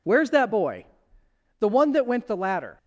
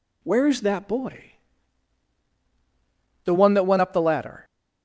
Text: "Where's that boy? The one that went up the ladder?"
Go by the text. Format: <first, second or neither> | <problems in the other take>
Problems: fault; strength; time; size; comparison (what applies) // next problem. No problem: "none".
second | skips "up"; at 2.2 s